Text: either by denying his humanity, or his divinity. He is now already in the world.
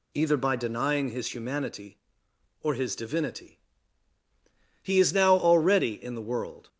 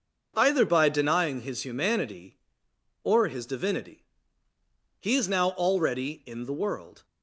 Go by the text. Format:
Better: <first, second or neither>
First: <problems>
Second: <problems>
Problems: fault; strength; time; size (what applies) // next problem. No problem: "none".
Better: neither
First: none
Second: none